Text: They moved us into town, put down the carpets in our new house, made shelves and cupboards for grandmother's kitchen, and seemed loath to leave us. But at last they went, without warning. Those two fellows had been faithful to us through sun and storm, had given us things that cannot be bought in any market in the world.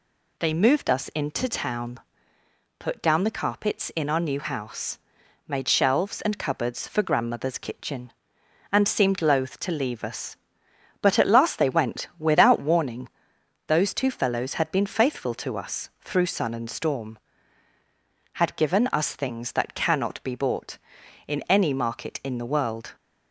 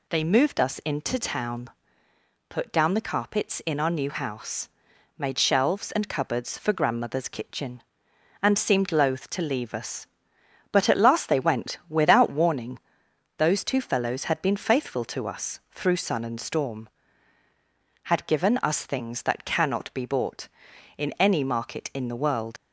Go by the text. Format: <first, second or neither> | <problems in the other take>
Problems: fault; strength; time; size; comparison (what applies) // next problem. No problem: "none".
first | leaves "world" unfinished; at 22.5 s; 90 ms